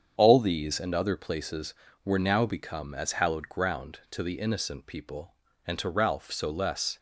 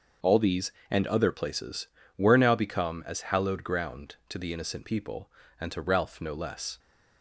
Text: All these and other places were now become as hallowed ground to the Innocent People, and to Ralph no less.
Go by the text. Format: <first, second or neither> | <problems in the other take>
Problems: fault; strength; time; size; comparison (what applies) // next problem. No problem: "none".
second | starts louder than the rest; strong; until 1.1 s; 7.5 dB; also in the second // says "so" for "no"; at 6.3 s